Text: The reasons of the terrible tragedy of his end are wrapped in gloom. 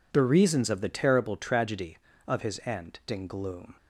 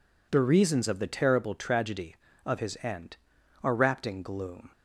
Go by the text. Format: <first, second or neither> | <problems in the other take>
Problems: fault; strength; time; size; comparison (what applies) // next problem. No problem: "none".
second | skips "are wrapped"; at 3.0 s